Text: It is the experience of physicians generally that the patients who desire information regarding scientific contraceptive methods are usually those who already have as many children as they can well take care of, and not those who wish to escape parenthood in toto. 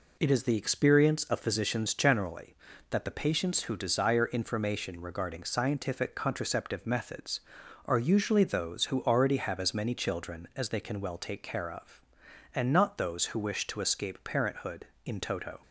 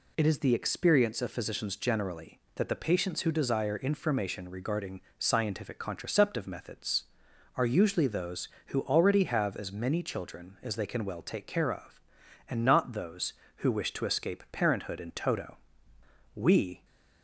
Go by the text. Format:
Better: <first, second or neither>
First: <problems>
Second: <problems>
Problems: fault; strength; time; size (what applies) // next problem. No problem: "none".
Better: first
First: none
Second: pauses between "regarding" and "scientific"; slight; at 5.0 s; 0.18 s long // goes on to say "We"; from 16.3 s on; 0.50 s long